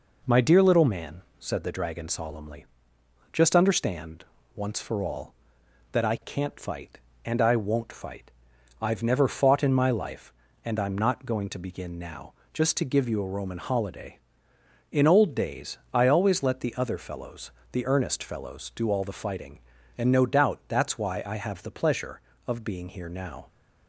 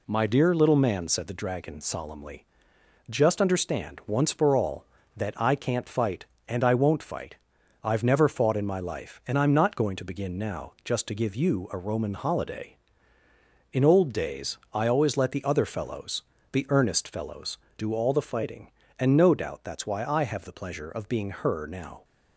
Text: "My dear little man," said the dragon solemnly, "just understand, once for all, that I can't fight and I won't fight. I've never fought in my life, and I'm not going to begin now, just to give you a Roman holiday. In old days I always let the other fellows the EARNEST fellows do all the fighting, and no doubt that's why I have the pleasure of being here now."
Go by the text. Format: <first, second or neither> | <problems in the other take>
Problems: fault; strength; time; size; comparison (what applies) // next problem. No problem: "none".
first | pauses between "days" and "I"; slight; at 14.5 s; 0.16 s long // pauses between "fellows" and "the"; slight; at 16.2 s; 0.30 s long; slight in the first // says "her" for "here"; at 21.2 s